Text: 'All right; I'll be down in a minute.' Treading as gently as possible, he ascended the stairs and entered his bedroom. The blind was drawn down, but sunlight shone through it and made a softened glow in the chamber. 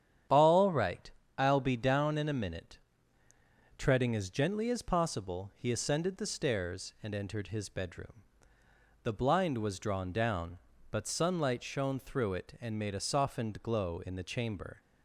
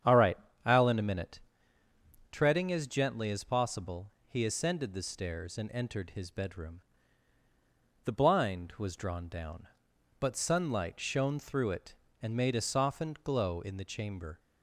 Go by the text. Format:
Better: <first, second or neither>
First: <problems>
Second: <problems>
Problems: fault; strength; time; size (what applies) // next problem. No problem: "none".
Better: first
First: starts louder than the rest; strong; until 1.5 s; 9.5 dB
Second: starts louder than the rest; strong; until 1.3 s; 8.5 dB // skips "be down"; at 0.8 s